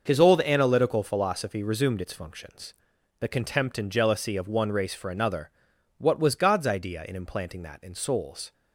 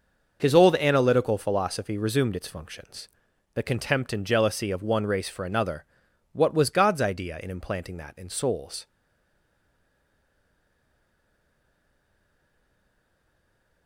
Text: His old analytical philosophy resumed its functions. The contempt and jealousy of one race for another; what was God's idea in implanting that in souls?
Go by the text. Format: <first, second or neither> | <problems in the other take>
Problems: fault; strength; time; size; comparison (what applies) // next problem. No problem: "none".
first | stays silent after the last word; strong; from 8.8 s on; 5.0 s long